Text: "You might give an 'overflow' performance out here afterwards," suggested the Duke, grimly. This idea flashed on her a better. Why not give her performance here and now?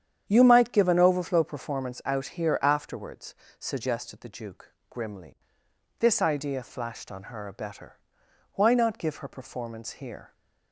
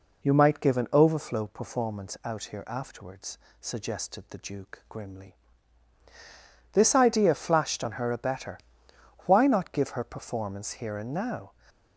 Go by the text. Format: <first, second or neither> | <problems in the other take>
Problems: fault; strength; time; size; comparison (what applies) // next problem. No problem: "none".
second | starts louder than the rest; strong; until 1.2 s; 9 dB // stops before "and now"; at 10.3 s